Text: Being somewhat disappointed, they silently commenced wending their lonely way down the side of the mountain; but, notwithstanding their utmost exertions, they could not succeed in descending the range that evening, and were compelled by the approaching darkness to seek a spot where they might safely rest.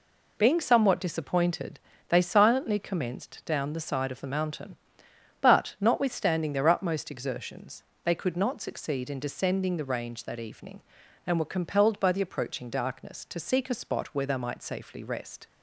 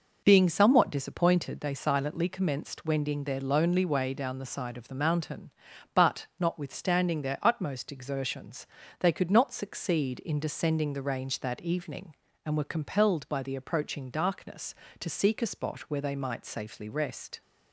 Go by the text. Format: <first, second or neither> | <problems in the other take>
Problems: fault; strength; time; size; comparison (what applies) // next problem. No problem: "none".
second | skips "wending their lonely way"; at 3.4 s